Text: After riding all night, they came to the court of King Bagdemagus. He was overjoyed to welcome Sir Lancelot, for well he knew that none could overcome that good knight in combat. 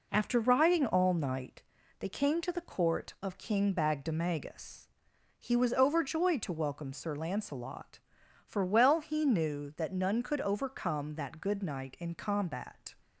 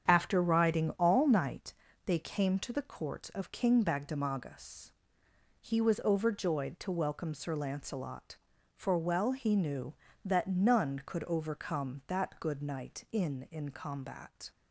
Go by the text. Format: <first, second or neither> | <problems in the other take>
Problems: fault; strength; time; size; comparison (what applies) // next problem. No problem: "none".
first | starts louder than the rest; strong; until 1.0 s; 7.5 dB // says "in" twice; at 13.5 s